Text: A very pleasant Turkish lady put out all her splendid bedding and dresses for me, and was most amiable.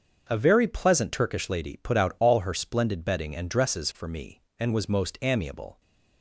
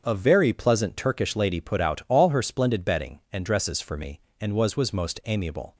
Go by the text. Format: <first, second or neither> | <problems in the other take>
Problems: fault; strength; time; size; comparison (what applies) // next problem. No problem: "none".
first | starts louder than the rest; strong; until 1.0 s; 7 dB; also in the first // says "was" twice; at 4.7 s